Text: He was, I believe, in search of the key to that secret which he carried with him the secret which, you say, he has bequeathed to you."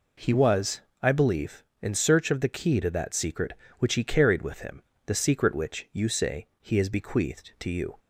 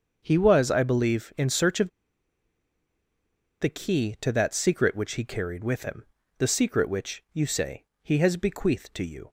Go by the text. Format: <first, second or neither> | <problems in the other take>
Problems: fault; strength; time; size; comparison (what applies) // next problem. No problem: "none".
first | starts louder than the rest; until 1.2 s; 6.5 dB // pauses between "of" and "the"; strong; at 1.8 s; 1.7 s long // pauses between "him" and "the"; slight; at 6.0 s; 0.34 s long; slight in the first